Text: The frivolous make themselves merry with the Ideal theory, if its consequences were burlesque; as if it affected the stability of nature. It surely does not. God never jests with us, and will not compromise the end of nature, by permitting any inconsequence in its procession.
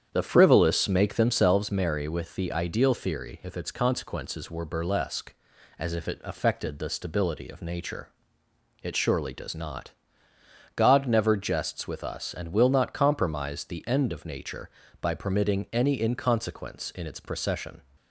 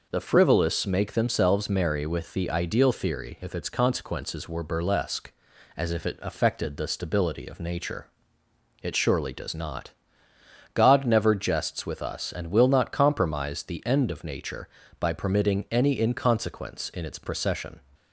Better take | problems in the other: second | starts louder than the rest; strong; until 1.7 s; 8.5 dB

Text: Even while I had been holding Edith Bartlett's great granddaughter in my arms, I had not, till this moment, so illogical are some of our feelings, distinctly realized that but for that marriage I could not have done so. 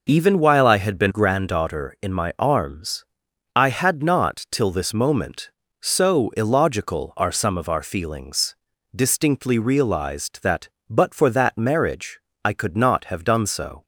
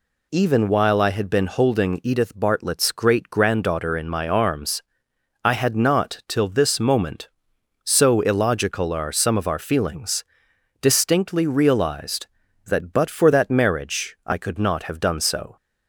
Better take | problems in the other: second | skips "holding Edith Bartlett's great"; at 1.1 s // pauses between "marriage" and "I"; slight; at 12.1 s; 0.26 s long

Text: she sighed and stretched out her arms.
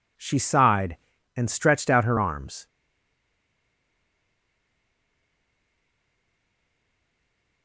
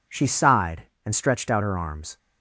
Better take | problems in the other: second | stays silent after the last word; strong; from 2.6 s on; 5.0 s long

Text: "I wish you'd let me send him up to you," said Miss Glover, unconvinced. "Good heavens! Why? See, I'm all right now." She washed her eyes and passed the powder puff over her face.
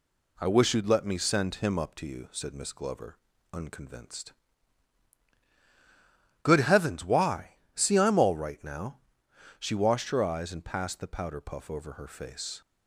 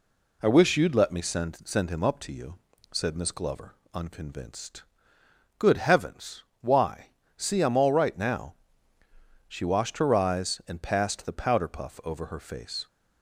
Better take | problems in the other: first | says "send" twice; at 1.6 s

